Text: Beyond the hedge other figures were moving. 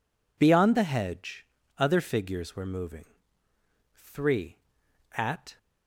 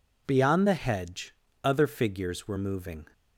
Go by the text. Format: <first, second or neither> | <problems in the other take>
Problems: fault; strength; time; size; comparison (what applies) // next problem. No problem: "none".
second | pauses between "hedge" and "other"; slight; at 1.4 s; 0.34 s long; slight in the second // goes on to say "Three at"; from 3.9 s on; 1.6 s long